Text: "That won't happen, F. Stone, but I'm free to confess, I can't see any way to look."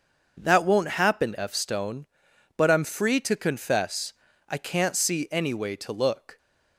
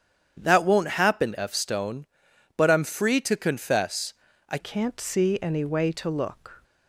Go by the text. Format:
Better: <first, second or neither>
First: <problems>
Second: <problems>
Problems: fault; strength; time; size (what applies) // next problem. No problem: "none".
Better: first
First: none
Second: starts louder than the rest; strong; until 1.4 s; 9 dB // changes voice at "can't"; from 4.5 s on; 2.1 s long